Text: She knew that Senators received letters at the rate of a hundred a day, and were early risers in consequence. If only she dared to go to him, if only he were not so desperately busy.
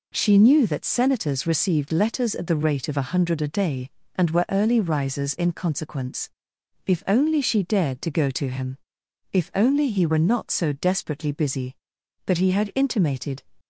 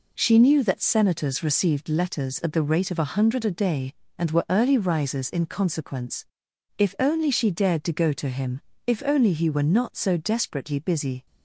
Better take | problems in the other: second | goes on to say "But he had intimated"; noticeable; from 12.2 s on; 1.1 s long

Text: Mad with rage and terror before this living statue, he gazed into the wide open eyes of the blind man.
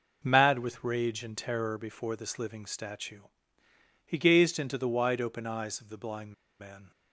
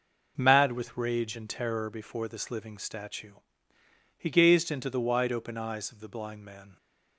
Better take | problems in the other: second | pauses between "blind" and "man"; slight; at 6.3 s; 0.28 s long

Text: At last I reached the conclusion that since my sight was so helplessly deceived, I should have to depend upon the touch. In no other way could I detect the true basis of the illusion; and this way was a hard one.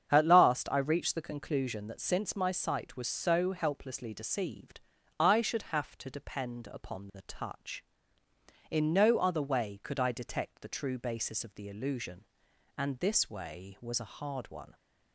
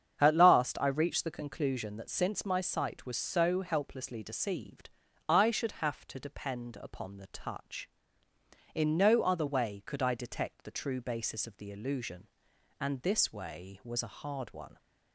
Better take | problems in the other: neither | starts louder than the rest; strong; the same in both

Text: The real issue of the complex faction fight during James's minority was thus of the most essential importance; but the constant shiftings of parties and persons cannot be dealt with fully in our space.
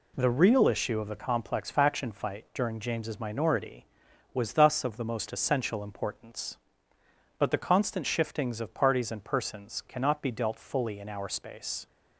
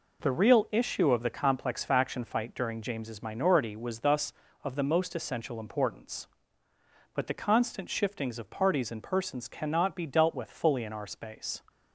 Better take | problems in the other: second | skips "with"; at 10.5 s

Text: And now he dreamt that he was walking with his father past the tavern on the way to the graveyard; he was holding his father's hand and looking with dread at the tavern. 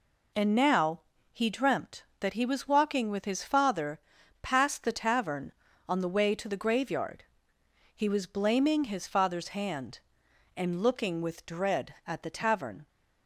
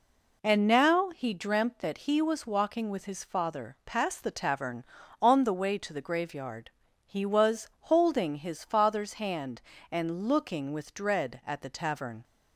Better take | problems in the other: second | pauses between "now" and "he"; slight; at 1.0 s; 0.30 s long // pauses between "father" and "past"; at 3.9 s; 0.42 s long // says "blaming" for "holding"; at 8.2 s

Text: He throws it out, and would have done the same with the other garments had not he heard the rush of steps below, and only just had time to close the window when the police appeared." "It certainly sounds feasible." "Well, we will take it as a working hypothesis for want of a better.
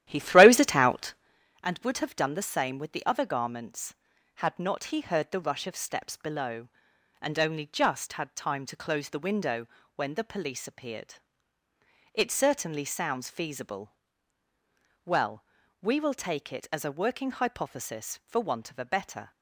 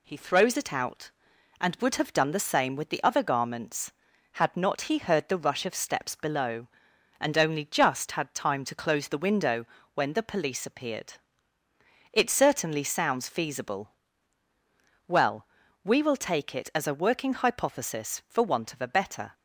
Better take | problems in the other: second | starts louder than the rest; strong; until 1.3 s; 12.5 dB // pauses between "window" and "when"; slight; at 9.6 s; 0.30 s long; slight in the second

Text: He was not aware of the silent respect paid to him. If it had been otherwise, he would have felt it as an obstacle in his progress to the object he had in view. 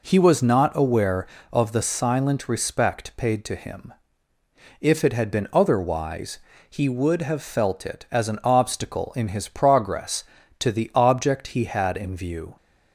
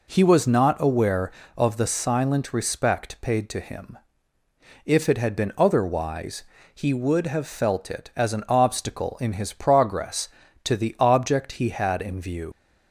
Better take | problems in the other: first | leaves "view" unfinished; at 12.5 s; 90 ms

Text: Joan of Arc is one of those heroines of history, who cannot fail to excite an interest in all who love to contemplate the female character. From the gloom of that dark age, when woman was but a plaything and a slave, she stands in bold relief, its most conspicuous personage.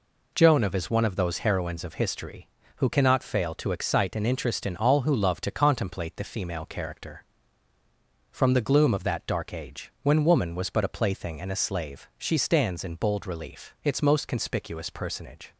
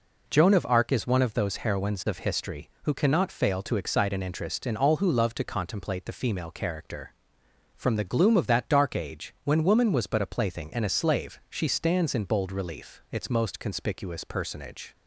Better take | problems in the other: second | skips "Arc"; at 0.7 s

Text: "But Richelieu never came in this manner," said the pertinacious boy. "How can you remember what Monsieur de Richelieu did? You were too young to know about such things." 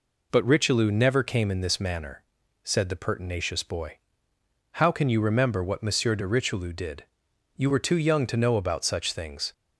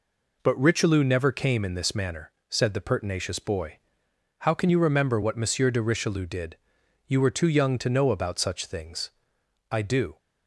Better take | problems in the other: first | goes on to say "I do"; slight; from 9.7 s on; 0.46 s long

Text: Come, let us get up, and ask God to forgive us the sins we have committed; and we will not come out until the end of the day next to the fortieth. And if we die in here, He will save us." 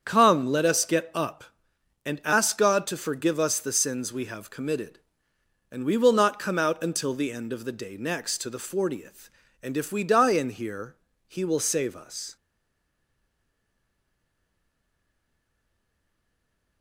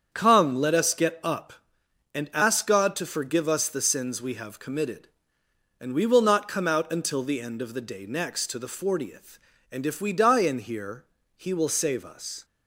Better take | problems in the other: second | starts louder than the rest; strong; until 1.0 s; 7.5 dB; strong in the second // stays silent after the last word; strong; from 12.3 s on; 4.5 s long

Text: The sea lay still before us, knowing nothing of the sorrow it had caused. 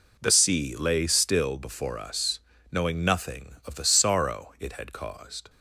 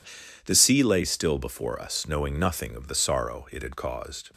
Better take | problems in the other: neither | none

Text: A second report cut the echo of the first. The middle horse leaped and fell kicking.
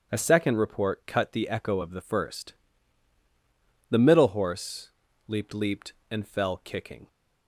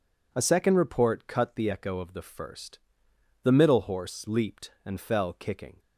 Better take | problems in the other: second | starts louder than the rest; strong; until 1.1 s; 8.5 dB // pauses between "horse" and "leaped"; slight; at 4.9 s; 0.36 s long // says "leaped" twice; at 5.5 s

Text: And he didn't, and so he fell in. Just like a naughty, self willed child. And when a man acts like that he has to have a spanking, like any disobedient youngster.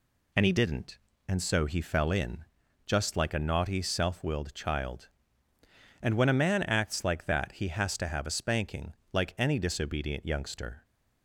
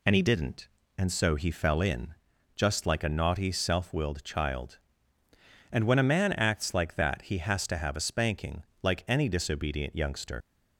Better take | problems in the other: first | leaves "youngster" unfinished; at 10.4 s; 135 ms

